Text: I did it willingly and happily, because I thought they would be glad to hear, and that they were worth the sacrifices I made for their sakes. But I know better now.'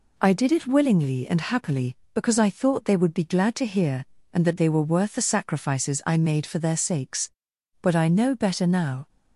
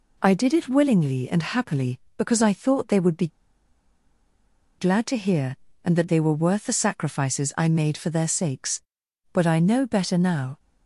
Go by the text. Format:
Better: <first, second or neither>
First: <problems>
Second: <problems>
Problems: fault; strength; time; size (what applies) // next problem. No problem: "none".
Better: first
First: none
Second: pauses between "be" and "glad"; strong; at 3.2 s; 1.5 s long